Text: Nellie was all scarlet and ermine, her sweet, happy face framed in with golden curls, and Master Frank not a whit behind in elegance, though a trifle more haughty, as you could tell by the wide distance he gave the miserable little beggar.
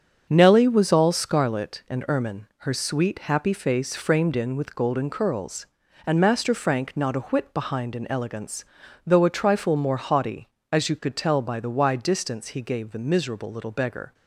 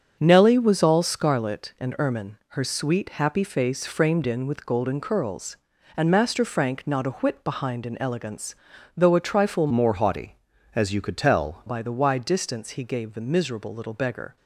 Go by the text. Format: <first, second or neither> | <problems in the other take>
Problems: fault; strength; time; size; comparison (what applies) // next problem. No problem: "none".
first | starts louder than the rest; strong; until 1.2 s; 7 dB; strong in the first // changes voice from "more" to "tell"; from 9.7 to 11.6 s; 1.9 s long